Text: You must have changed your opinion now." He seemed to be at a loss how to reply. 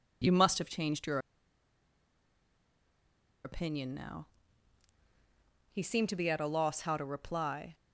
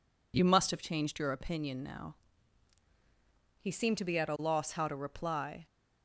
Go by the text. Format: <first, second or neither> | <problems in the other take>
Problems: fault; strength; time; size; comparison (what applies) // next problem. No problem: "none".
second | pauses between "your" and "opinion"; strong; at 1.1 s; 2.2 s long